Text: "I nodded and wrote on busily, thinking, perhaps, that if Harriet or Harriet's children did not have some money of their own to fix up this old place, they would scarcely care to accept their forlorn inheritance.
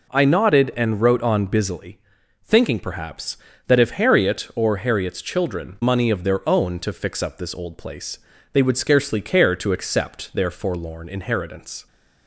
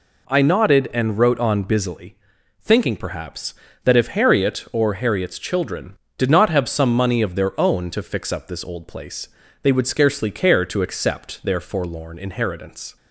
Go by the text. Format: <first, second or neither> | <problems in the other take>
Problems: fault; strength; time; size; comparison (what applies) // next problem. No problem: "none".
second | skips "did not have some"; at 5.8 s